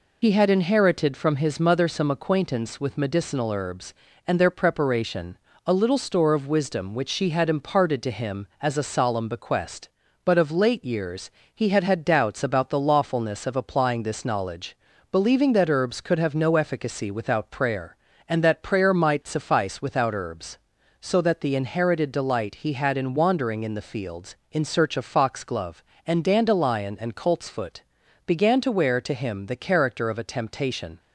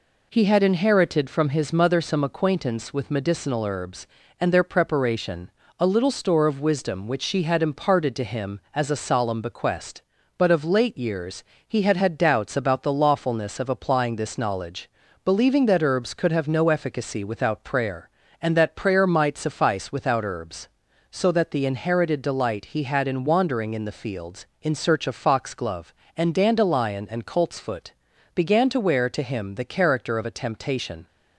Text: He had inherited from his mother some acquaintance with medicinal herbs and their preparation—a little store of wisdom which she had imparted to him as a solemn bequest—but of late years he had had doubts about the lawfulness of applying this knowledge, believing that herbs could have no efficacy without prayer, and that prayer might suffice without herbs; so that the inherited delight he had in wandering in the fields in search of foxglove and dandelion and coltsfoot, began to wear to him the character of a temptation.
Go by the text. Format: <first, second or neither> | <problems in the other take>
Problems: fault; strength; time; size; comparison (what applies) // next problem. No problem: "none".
second | loses the start of "He"; at 0.2 s; 40 ms // pauses between "years" and "he"; slight; at 11.2 s; 0.24 s long; slight in the second